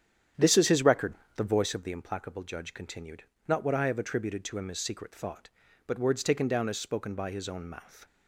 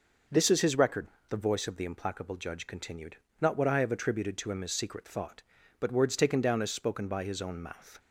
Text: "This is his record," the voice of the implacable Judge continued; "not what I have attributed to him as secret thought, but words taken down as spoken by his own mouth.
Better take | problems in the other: second | starts louder than the rest; strong; until 1.9 s; 9 dB

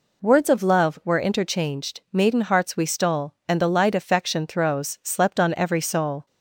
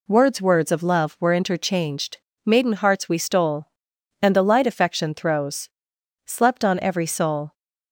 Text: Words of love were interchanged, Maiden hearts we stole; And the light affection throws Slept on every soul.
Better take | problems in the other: first | says "Words" twice; at 0.3 s // pauses between "throws" and "Slept"; noticeable; at 5.6 s; 0.56 s long

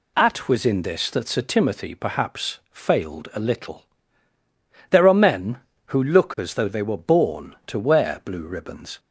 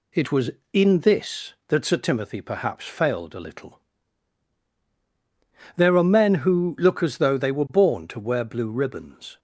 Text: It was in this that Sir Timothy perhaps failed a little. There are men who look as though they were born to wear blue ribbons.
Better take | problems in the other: second | says "At" for "It"; at 0.1 s

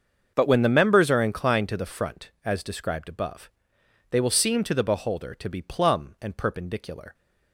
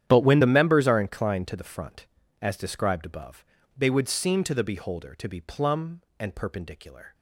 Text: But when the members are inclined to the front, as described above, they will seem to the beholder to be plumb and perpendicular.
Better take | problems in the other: first | starts louder than the rest; strong; until 1.0 s; 10 dB; also in the first // says "would" for "will"; at 3.8 s

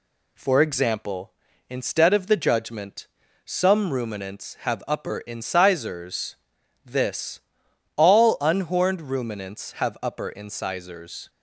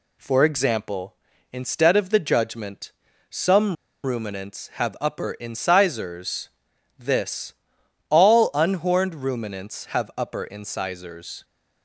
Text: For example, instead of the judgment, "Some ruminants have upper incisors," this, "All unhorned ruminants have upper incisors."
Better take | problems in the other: first | pauses between "Some" and "ruminants"; slight; at 3.7 s; 0.30 s long

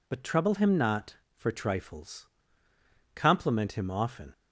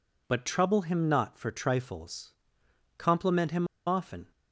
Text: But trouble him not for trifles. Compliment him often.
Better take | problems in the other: first | pauses between "him" and "often"; slight; at 3.6 s; 0.21 s long

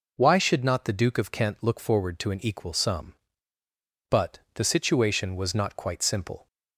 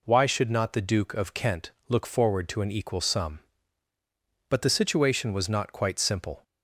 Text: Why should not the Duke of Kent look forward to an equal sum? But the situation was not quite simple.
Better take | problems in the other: neither | none

